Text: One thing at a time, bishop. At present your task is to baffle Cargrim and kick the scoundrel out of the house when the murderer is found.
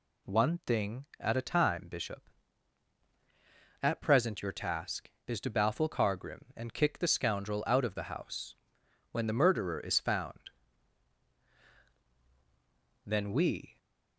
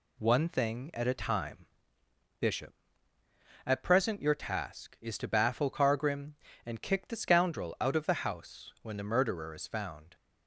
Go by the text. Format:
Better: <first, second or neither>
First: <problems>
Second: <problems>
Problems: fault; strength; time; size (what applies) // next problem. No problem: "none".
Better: second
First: pauses between "house" and "when"; noticeable; at 8.5 s; 0.56 s long // goes on to say "Then we"; noticeable; from 13.0 s on; 0.72 s long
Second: none